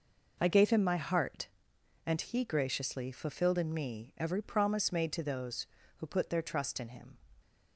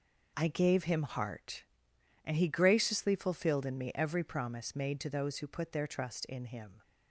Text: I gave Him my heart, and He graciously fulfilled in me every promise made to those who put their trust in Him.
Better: first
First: none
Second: skips "my"; at 1.0 s

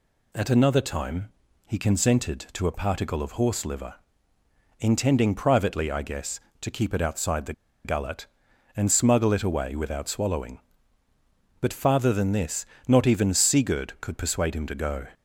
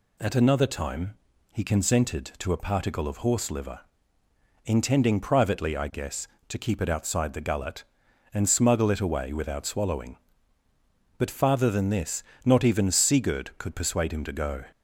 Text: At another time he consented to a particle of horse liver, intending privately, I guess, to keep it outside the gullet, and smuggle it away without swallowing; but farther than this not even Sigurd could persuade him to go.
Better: second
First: pauses between "time" and "he"; slight; at 1.3 s; 0.36 s long // pauses between "the" and "gullet"; slight; at 7.5 s; 0.32 s long // pauses between "this" and "not"; slight; at 12.6 s; 0.22 s long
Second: pauses between "time" and "he"; slight; at 1.1 s; 0.36 s long // pauses between "this" and "not"; slight; at 12.2 s; 0.22 s long

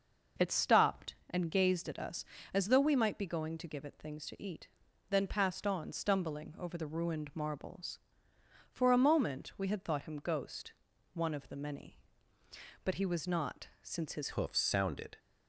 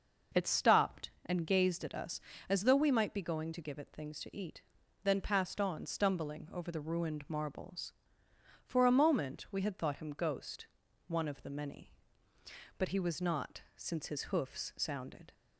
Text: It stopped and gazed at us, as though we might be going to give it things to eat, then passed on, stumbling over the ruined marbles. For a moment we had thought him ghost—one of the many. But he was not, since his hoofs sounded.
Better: second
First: changes voice at "hoofs"; from 14.3 s on; 0.8 s long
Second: none

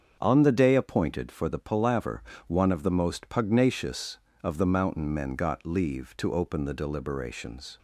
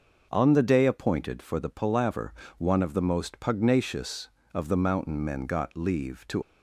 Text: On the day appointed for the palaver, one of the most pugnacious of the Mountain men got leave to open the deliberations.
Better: first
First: starts louder than the rest; strong; until 1.2 s; 7 dB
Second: starts louder than the rest; noticeable; until 1.3 s; 6 dB // stops before "open the deliberations"; at 6.4 s

